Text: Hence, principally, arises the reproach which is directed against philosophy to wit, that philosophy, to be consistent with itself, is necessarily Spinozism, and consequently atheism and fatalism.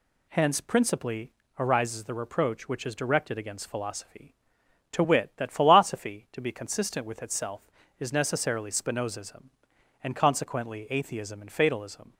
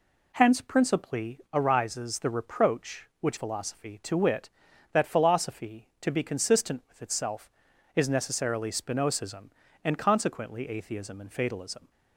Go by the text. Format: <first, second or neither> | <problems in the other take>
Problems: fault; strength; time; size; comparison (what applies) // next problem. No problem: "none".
first | skips "is directed against"; at 3.3 s